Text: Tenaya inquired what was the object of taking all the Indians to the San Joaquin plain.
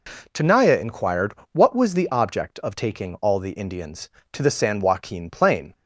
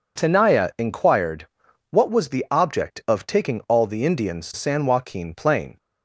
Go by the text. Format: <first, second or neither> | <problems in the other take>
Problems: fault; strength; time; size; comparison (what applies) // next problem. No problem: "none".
first | pauses between "inquired" and "what"; at 1.4 s; 0.44 s long; slight in the first // skips "to the"; at 4.5 s